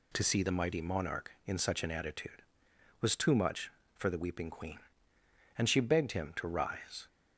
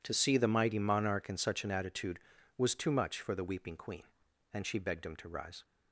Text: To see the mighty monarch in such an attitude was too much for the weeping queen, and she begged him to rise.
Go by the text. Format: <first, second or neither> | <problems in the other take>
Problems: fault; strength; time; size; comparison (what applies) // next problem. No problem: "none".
neither | none